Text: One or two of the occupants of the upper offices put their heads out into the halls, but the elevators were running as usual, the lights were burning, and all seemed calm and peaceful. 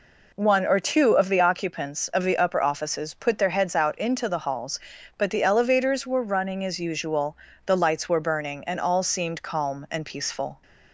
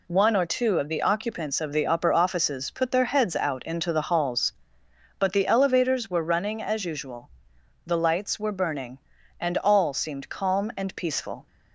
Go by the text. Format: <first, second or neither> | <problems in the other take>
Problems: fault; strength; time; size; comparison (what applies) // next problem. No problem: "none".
neither | none